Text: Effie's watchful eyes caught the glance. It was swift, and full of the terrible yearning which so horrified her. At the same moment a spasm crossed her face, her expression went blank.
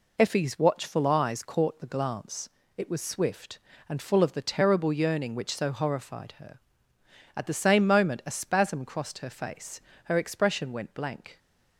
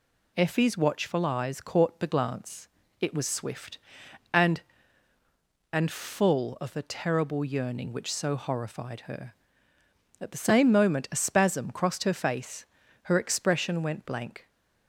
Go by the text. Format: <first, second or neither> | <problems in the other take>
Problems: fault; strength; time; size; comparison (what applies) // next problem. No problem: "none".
first | says "and" twice; at 5.7 s